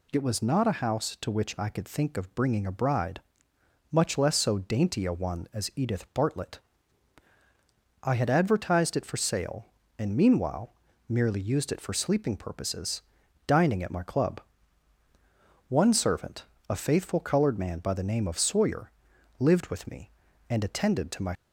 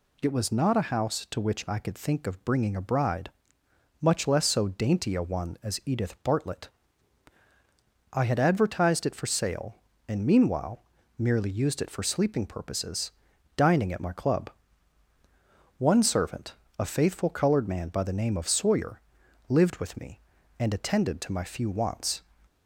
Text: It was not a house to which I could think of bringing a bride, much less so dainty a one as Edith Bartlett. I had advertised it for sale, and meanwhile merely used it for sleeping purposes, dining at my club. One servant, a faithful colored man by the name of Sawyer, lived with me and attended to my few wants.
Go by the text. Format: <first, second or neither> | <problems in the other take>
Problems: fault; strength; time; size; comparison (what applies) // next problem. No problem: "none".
second | pauses between "meanwhile" and "merely"; slight; at 10.7 s; 0.36 s long; slight in the second // stops before "few wants"; at 21.3 s